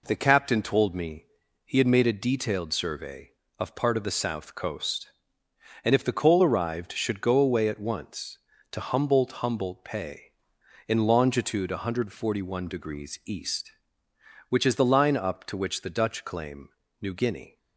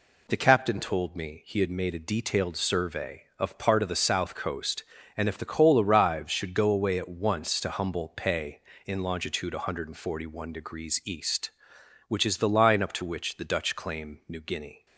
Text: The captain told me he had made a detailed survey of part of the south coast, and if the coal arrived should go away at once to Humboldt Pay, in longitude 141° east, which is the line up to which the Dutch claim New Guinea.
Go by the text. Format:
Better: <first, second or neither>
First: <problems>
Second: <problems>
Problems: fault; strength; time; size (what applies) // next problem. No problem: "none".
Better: second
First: pauses between "me" and "he"; at 1.2 s; 0.40 s long // says "Humboldt" twice; at 9.4 s // pauses between "claim" and "New"; slight; at 16.6 s; 0.30 s long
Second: none